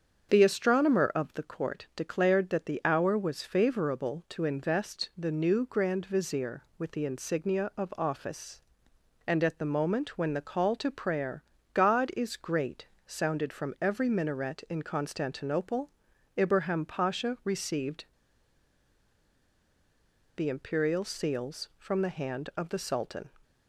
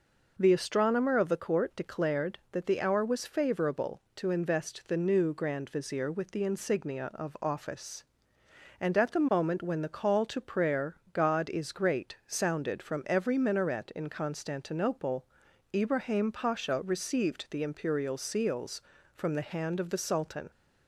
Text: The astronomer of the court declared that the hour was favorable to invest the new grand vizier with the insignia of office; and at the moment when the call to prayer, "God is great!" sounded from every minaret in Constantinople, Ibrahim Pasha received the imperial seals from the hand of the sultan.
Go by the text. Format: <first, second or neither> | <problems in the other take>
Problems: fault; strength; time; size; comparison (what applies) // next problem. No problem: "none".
second | starts louder than the rest; until 1.3 s; 7 dB // pauses between "received" and "the"; strong; at 18.0 s; 2.3 s long